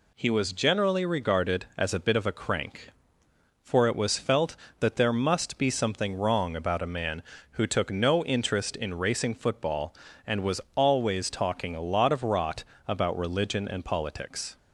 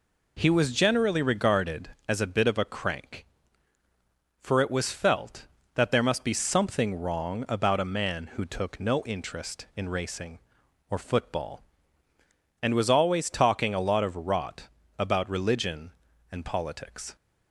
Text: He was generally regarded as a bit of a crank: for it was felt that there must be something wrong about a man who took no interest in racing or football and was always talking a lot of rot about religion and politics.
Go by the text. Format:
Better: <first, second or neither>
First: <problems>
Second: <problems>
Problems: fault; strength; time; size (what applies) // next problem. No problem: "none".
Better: second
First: skips "or"; at 9.3 s // pauses between "was" and "always"; slight; at 10.6 s; 0.16 s long // pauses between "rot" and "about"; slight; at 12.6 s; 0.24 s long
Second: pauses between "rot" and "about"; slight; at 14.6 s; 0.32 s long